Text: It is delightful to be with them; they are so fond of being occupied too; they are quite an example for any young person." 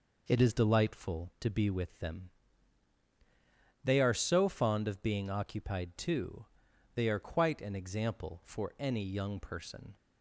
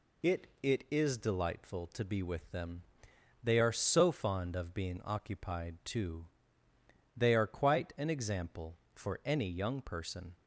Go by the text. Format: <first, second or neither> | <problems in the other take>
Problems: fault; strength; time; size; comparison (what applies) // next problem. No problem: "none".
first | says "It" twice; at 0.6 s